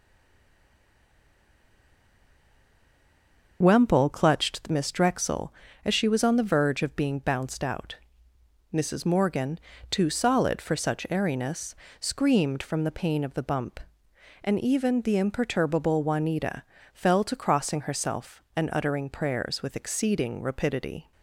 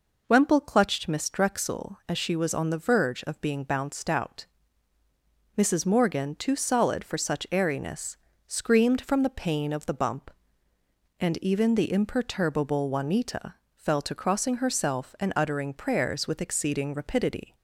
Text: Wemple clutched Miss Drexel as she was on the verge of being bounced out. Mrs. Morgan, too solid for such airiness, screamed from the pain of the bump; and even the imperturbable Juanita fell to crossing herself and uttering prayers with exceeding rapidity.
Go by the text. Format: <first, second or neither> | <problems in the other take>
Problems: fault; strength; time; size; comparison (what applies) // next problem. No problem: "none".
second | stays silent before the first word; strong; until 3.6 s; 3.6 s long // starts louder than the rest; until 4.6 s; 6 dB // pauses between "Juanita" and "fell"; slight; at 16.6 s; 0.32 s long; slight in the second